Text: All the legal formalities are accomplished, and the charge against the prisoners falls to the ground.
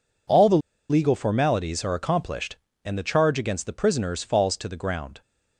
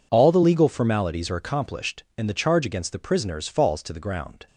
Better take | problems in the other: second | pauses between "the" and "legal"; slight; at 0.5 s; 0.31 s long

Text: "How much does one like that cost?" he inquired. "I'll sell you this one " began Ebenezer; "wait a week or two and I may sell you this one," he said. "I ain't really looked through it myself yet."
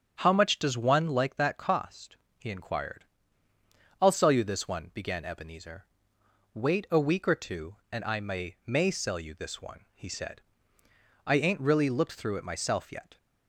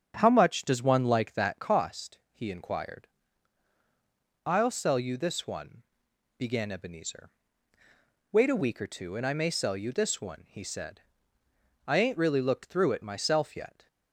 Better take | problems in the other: second | starts louder than the rest; strong; until 1.2 s; 7.5 dB; strong in the second // says "may" twice; at 8.6 s

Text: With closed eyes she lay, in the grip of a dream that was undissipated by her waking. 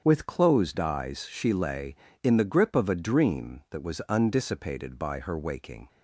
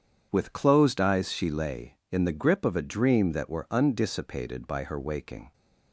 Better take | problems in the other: first | starts louder than the rest; strong; until 1.3 s; 8 dB; strong in the first // says "were" for "was"; at 3.4 s

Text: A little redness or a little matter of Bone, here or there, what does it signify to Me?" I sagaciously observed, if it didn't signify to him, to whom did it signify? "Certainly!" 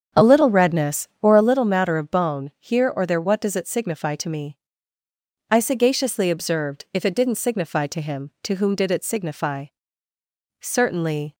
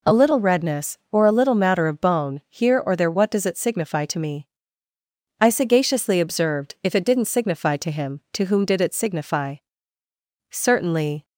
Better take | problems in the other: second | starts louder than the rest; strong; until 1.6 s; 7.5 dB

